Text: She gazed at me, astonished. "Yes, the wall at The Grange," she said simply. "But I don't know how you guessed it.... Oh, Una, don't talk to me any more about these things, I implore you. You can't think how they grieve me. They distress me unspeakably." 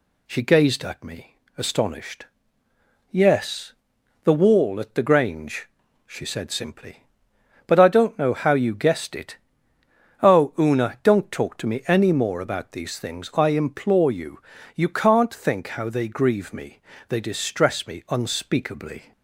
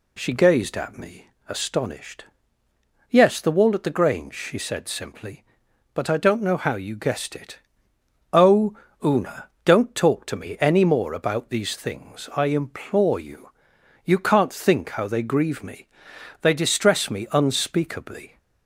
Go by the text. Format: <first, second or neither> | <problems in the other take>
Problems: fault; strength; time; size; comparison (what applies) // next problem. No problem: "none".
neither | none